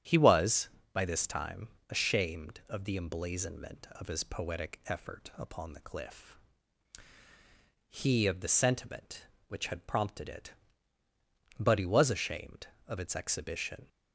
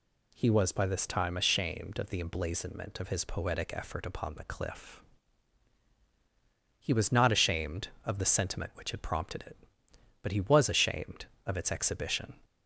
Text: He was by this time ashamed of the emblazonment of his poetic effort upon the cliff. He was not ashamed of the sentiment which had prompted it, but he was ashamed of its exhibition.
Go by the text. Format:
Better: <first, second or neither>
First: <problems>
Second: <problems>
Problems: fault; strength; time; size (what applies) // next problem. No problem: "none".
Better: second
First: starts louder than the rest; strong; until 1.2 s; 9.5 dB // pauses between "time" and "ashamed"; slight; at 1.6 s; 0.24 s long // skips "was not ashamed"; at 8.2 s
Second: none